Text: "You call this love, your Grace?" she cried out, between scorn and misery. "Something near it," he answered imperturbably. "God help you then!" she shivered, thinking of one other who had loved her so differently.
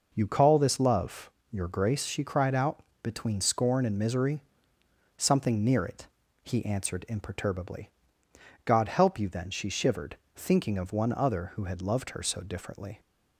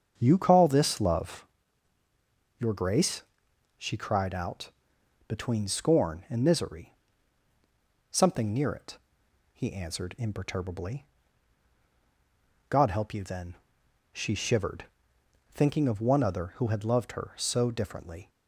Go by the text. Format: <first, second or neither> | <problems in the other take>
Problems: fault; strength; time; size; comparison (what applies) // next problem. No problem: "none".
first | starts louder than the rest; strong; until 1.5 s; 7.5 dB